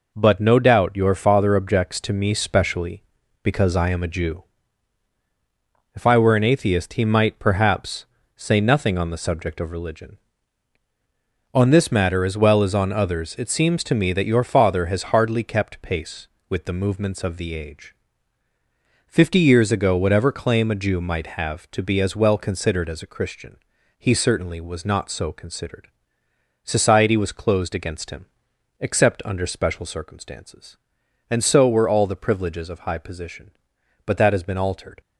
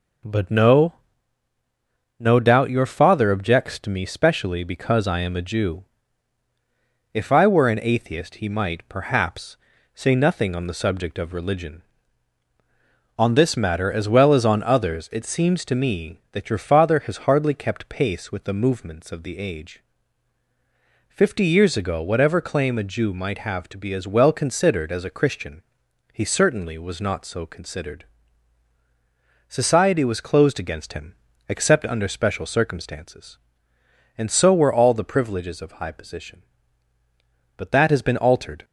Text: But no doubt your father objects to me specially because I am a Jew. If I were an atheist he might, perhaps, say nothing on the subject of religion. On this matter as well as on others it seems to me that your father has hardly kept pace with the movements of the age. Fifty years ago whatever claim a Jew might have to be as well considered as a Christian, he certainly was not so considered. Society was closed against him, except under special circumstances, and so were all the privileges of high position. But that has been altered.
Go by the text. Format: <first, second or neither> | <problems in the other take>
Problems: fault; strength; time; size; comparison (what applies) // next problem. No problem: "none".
first | says "no" twice; at 2.1 s